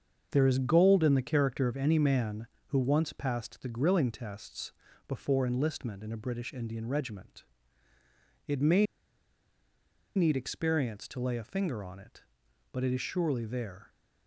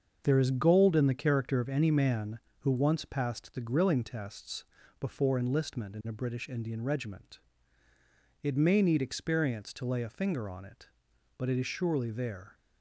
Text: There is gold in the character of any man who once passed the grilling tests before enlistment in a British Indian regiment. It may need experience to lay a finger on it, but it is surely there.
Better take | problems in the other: second | starts louder than the rest; until 1.3 s; 6.5 dB; also in the second // pauses between "tests" and "before"; slight; at 4.7 s; 0.36 s long; slight in the second // pauses between "may" and "need"; strong; at 8.8 s; 1.3 s long

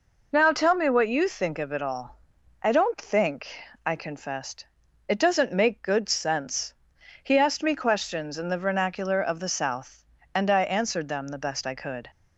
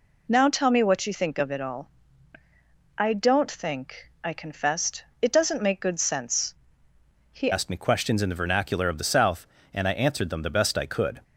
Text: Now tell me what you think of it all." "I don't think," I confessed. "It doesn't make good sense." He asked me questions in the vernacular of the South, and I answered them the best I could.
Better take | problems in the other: first | changes voice at "asked"; from 7.5 s on; 3.7 s long

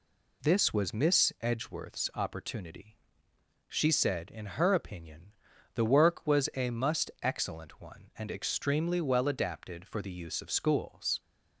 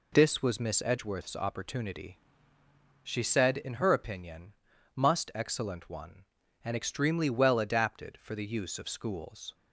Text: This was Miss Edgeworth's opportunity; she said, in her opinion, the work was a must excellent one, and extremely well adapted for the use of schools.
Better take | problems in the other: first | skips "the work was a"; at 4.7 s

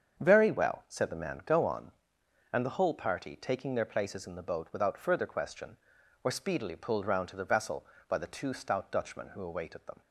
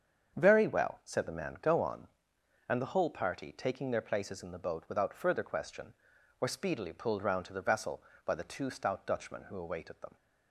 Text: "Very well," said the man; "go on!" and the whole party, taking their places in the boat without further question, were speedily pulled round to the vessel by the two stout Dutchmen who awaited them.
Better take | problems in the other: neither | starts louder than the rest; strong; the same in both

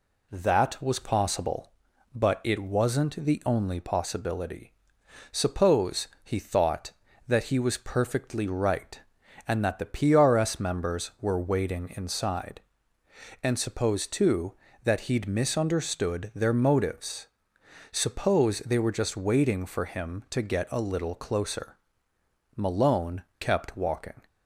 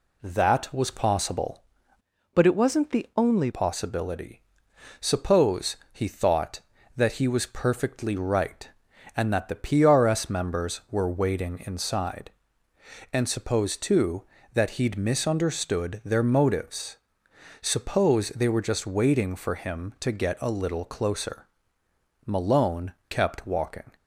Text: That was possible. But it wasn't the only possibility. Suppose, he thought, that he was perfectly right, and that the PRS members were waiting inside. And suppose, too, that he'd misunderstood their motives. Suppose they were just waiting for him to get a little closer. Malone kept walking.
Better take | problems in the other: first | changes voice from "But" to "only"; from 2.3 to 3.4 s; 1.1 s long // pauses between "Malone" and "kept"; slight; at 22.9 s; 0.18 s long; slight in the first

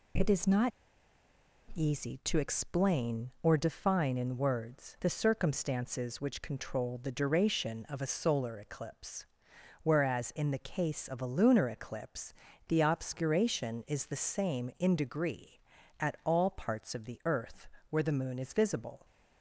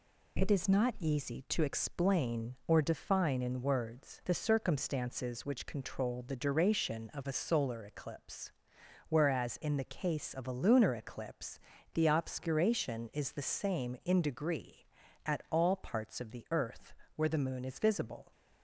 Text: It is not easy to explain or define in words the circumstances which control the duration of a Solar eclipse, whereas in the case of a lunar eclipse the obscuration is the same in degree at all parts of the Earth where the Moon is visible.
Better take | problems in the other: second | pauses between "not" and "easy"; at 0.7 s; 1.0 s long // pauses between "eclipse" and "the"; slight; at 12.3 s; 0.34 s long; slight in the second // pauses between "Earth" and "where"; slight; at 17.6 s; 0.24 s long; slight in the second

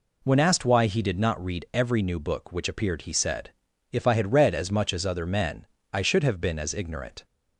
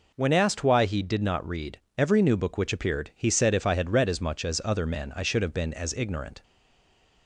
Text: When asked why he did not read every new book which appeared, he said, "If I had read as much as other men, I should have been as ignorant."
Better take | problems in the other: first | pauses between "read" and "every"; slight; at 1.7 s; 0.18 s long // stays silent after the last word; slight; from 6.4 s on; 0.8 s long

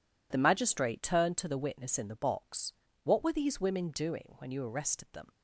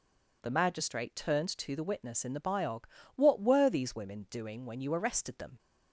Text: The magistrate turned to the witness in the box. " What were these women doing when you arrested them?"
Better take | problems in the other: first | says "biog" for "box"; at 2.3 s

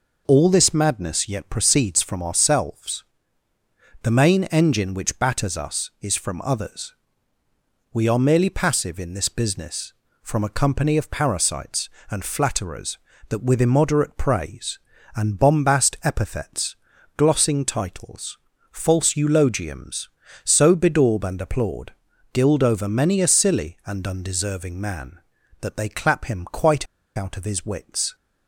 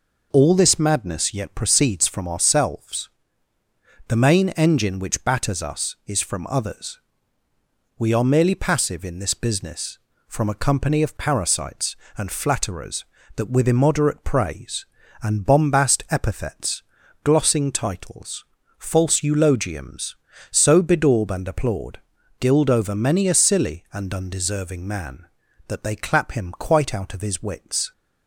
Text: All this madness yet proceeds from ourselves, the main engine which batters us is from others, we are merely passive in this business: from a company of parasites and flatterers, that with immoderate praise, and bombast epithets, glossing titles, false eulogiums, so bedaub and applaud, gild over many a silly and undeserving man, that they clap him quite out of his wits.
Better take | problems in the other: second | pauses between "quite" and "out"; slight; at 26.8 s; 0.31 s long

